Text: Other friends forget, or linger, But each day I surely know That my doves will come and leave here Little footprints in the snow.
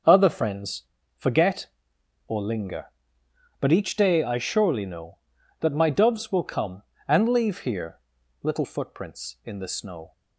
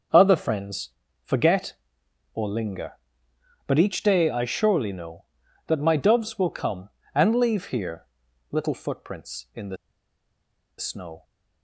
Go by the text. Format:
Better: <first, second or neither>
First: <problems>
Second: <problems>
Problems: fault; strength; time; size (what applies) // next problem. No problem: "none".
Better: first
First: starts louder than the rest; until 1.4 s; 6.5 dB // pauses between "friends" and "forget"; slight; at 0.8 s; 0.34 s long // pauses between "here" and "Little"; at 7.9 s; 0.42 s long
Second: starts louder than the rest; until 1.4 s; 6.5 dB // pauses between "friends" and "forget"; slight; at 0.8 s; 0.34 s long // pauses between "here" and "Little"; at 8.0 s; 0.44 s long // pauses between "the" and "snow"; at 9.7 s; 1.0 s long